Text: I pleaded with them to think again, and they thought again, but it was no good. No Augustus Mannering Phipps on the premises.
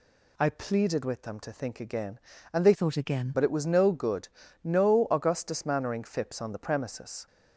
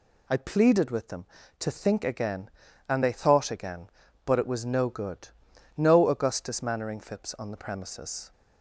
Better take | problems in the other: second | changes voice from "thought" to "again"; from 2.7 to 3.3 s; 0.6 s long

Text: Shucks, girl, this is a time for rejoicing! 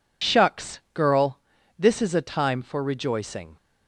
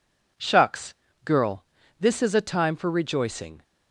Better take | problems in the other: second | loses the start of "Shucks"; at 0.2 s; 45 ms

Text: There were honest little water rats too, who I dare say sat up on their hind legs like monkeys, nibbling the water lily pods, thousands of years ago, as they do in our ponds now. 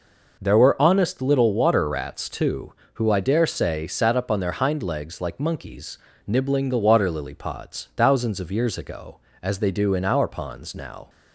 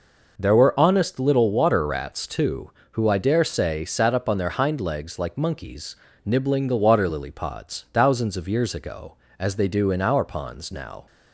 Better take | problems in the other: neither | none

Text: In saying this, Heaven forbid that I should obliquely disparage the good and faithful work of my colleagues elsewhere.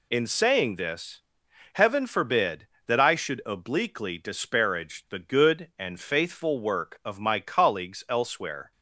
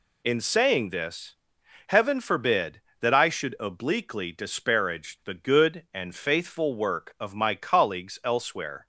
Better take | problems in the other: neither | none

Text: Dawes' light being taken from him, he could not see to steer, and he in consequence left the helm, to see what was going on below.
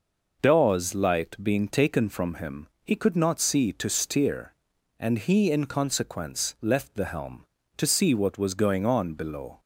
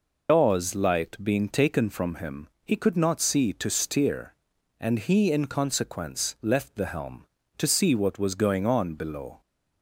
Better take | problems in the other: first | loses the start of "Dawes"; at 0.2 s; 75 ms

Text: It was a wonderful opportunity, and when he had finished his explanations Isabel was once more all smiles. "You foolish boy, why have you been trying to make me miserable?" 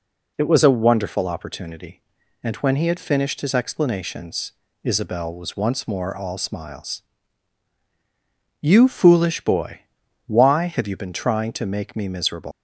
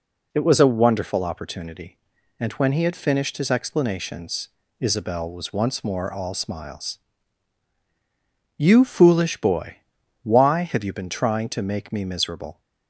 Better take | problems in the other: second | pauses between "explanations" and "Isabel"; slight; at 4.5 s; 0.32 s long; slight in the second // leaves "miserable" unfinished; at 12.5 s; 125 ms

